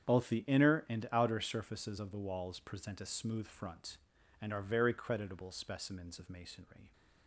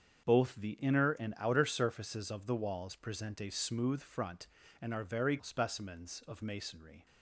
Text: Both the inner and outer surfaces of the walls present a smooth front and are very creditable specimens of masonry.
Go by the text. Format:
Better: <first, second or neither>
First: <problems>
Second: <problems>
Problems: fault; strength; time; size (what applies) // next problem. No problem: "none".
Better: first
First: starts louder than the rest; strong; until 1.1 s; 8.5 dB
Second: starts louder than the rest; strong; until 1.2 s; 7 dB // skips "creditable"; at 5.4 s